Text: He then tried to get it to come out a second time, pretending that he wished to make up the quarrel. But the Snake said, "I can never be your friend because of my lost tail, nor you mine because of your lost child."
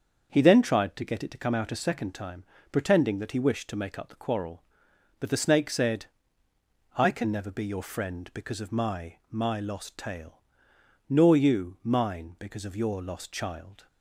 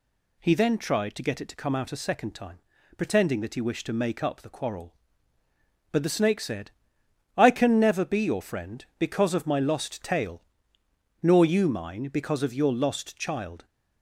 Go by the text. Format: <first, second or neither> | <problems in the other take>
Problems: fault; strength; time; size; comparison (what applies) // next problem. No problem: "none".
second | starts louder than the rest; until 1.3 s; 6.5 dB // says "my" twice; at 9.2 s